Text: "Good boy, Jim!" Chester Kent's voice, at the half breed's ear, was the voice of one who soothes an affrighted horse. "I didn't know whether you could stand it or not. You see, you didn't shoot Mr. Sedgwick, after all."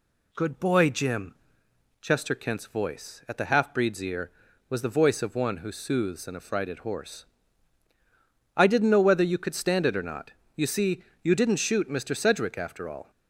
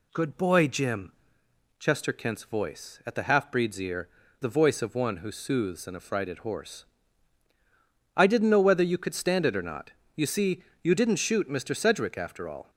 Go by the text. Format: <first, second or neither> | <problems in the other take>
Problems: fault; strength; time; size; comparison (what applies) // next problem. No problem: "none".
first | skips "was"; at 4.2 s